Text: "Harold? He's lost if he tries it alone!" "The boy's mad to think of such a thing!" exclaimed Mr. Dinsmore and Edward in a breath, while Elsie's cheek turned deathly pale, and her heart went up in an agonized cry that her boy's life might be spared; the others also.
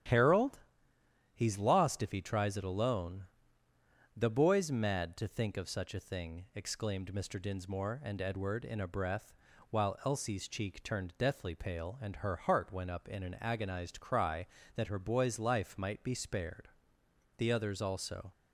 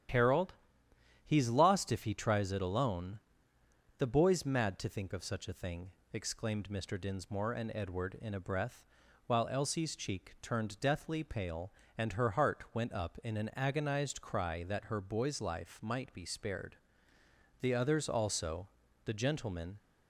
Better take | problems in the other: first | starts louder than the rest; strong; until 1.8 s; 10.5 dB; strong in the first // goes on to say "The gentlemen"; noticeable; from 19.0 s on; 0.74 s long

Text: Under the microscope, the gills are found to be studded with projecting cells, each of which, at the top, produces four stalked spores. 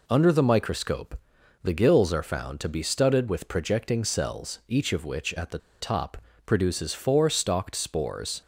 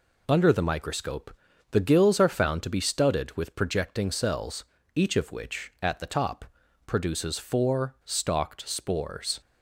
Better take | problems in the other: second | pauses between "the" and "top"; slight; at 5.5 s; 0.22 s long

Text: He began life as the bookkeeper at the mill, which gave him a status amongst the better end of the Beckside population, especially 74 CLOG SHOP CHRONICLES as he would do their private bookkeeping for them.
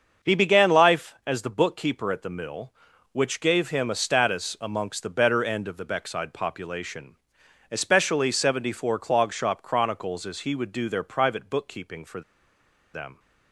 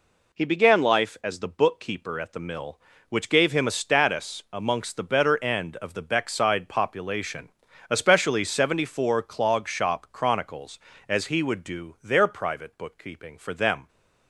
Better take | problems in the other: second | starts louder than the rest; until 1.3 s; 6.5 dB // pauses between "for" and "them"; noticeable; at 12.2 s; 0.73 s long

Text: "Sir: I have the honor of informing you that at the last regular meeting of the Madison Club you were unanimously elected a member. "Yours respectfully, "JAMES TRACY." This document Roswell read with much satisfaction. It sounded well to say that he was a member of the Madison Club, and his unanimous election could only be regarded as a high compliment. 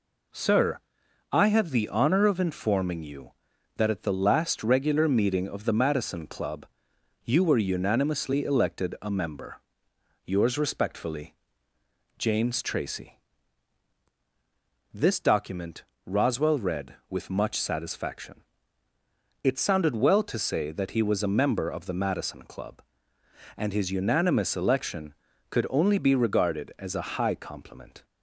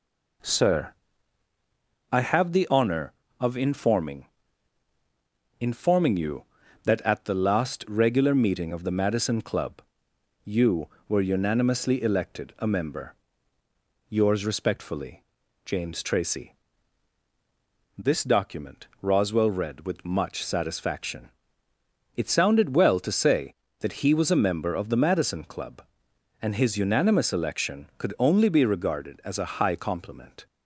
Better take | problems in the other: first | says "informing" twice; at 5.5 s // pauses between "Club" and "you"; noticeable; at 9.8 s; 0.62 s long; noticeable in the first // pauses between "document" and "Roswell"; slight; at 18.8 s; 0.16 s long; slight in the first

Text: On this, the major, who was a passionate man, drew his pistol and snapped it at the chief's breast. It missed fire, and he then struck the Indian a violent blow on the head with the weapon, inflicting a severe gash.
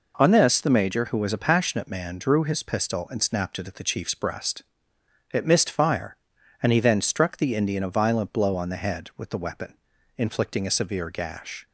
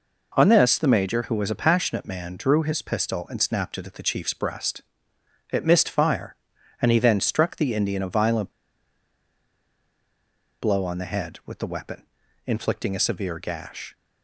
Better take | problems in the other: first | pauses between "violent" and "blow"; strong; at 8.5 s; 2.1 s long

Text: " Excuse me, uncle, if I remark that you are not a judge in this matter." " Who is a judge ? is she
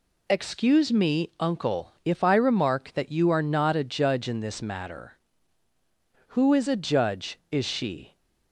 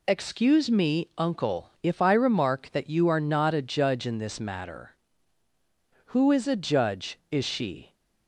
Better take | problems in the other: neither | none

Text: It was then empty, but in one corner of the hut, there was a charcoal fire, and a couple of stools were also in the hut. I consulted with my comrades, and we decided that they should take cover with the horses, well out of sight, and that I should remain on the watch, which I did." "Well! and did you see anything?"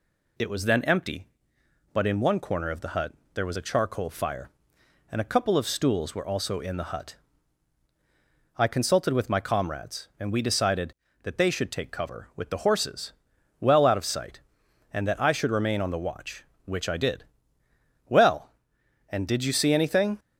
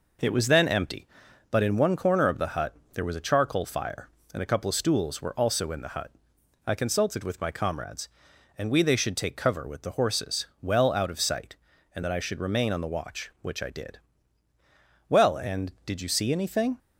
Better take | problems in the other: first | skips "decided that"; at 8.8 s

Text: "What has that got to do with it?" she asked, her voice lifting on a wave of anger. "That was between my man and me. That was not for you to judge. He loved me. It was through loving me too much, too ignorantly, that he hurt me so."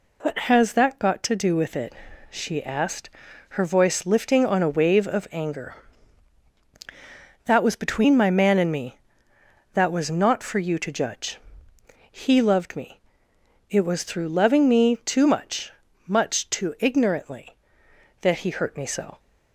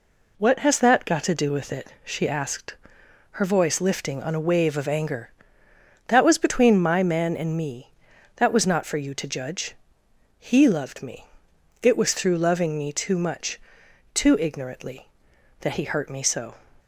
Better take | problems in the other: second | says "much" twice; at 16.0 s

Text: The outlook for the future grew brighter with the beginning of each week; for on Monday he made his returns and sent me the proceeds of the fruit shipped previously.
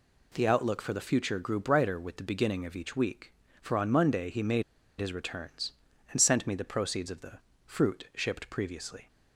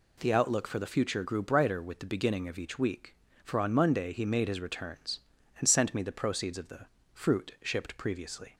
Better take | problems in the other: second | pauses between "made" and "his"; at 4.6 s; 0.36 s long // pauses between "the" and "fruit"; slight; at 7.3 s; 0.28 s long; slight in the second

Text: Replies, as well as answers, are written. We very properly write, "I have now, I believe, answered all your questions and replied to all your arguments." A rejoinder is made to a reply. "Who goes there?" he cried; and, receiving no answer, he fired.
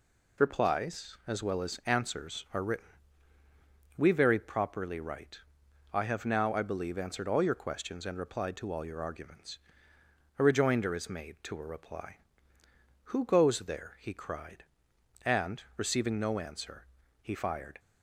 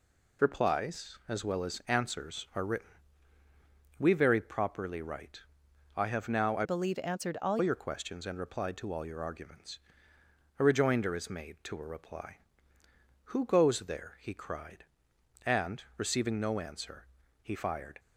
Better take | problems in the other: first | changes voice from "believe" to "all"; from 6.6 to 7.5 s; 0.9 s long

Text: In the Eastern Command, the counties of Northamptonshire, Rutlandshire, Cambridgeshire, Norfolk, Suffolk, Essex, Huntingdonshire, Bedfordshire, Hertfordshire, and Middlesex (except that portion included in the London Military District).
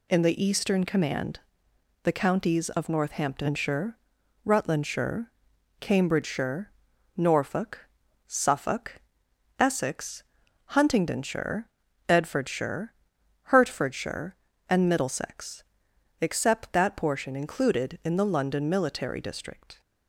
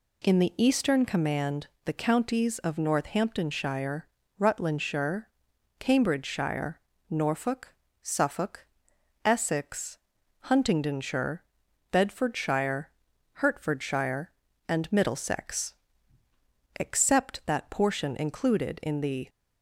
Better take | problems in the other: first | stops before "London Military District"; at 19.2 s

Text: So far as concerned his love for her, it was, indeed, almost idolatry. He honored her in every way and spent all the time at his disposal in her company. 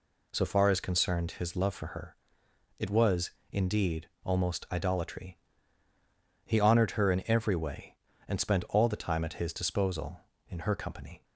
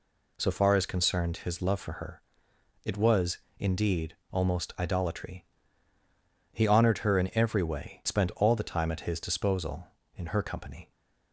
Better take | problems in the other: first | skips "and"; at 8.0 s

